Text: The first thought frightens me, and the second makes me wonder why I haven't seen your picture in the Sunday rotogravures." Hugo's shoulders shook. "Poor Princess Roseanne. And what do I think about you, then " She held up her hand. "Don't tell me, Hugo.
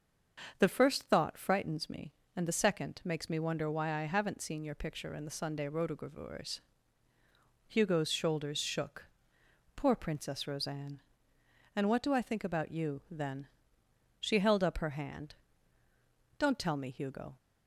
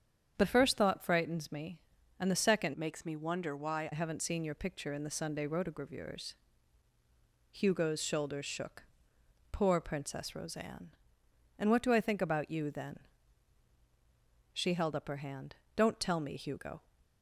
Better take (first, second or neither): first